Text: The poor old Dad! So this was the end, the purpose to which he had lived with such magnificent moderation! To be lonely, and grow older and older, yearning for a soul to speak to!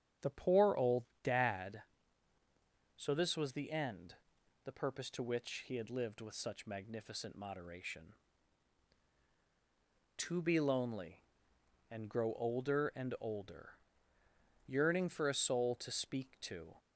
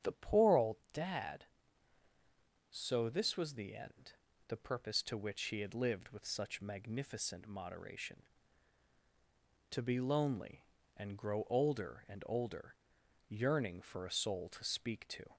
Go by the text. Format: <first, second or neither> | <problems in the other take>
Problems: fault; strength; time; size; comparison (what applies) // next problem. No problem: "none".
neither | starts louder than the rest; strong; the same in both // pauses between "old" and "Dad"; slight; the same in both